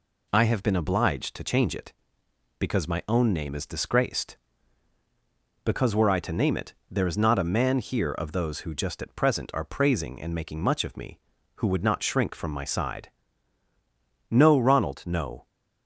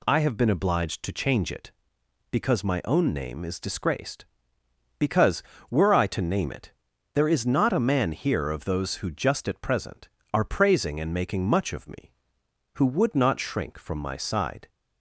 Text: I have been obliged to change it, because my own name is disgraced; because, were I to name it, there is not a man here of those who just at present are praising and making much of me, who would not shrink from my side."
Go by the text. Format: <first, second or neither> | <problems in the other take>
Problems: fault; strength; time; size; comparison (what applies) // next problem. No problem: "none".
second | goes on to say "No Ronald no"; noticeable; from 14.3 s on; 1.1 s long